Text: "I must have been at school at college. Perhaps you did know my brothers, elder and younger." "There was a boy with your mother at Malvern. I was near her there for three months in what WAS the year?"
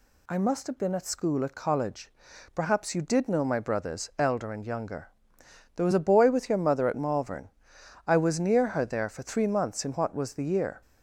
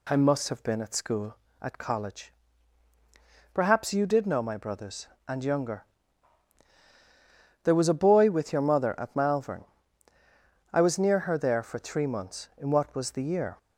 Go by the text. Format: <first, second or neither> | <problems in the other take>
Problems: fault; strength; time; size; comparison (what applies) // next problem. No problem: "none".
first | skips "elder"; at 5.1 s